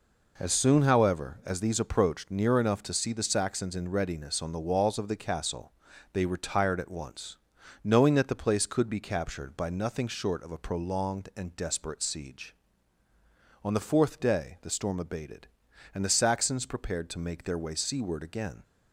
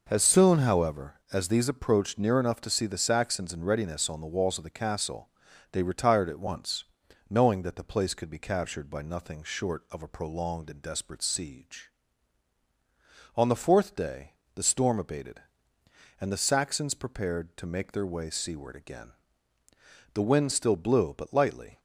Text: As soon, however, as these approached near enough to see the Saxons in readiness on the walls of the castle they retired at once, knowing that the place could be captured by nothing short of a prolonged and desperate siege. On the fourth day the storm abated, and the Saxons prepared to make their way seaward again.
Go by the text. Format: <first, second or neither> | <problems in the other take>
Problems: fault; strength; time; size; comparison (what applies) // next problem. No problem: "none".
first | pauses between "castle" and "they"; noticeable; at 5.2 s; 0.46 s long; also in the first // pauses between "day" and "the"; slight; at 14.3 s; 0.24 s long // goes on to say "The wind still blew but lightly"; from 20.1 s on; 1.6 s long